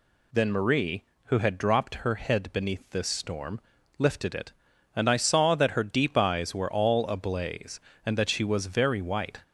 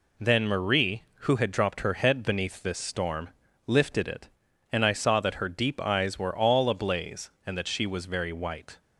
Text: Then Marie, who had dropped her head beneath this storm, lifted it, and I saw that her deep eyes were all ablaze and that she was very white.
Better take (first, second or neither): second